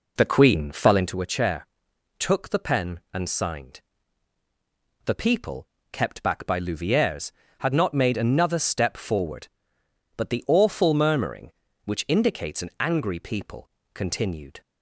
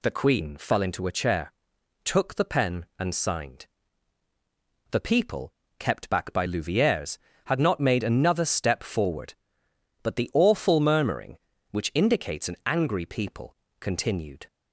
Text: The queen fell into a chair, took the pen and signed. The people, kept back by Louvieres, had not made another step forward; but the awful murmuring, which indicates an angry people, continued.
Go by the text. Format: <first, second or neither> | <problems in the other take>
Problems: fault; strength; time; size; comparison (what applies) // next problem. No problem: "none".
second | starts louder than the rest; until 1.2 s; 4 dB